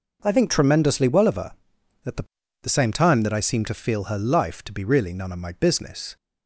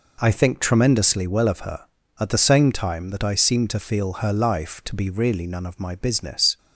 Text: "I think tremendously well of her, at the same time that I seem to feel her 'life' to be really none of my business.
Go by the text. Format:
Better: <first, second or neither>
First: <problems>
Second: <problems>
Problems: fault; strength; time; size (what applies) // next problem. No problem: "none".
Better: second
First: says "the" twice; at 2.6 s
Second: none